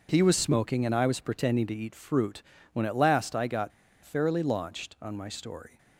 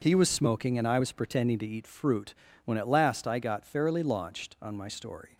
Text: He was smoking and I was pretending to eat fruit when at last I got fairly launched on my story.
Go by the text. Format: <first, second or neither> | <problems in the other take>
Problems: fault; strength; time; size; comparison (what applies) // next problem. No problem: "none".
second | pauses between "fruit" and "when"; slight; at 2.4 s; 0.32 s long; slight in the second // pauses between "got" and "fairly"; slight; at 3.7 s; 0.33 s long